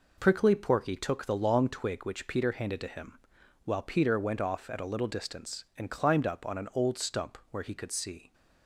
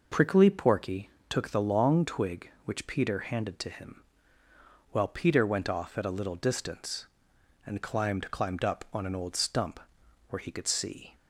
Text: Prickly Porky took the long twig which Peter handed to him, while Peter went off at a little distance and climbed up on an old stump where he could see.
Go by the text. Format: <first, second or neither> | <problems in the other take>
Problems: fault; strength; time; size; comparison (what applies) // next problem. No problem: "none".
first | pauses between "Porky" and "took"; slight; at 1.0 s; 0.22 s long // says "climbed" twice; at 8.3 s // pauses between "stump" and "where"; noticeable; at 9.7 s; 0.50 s long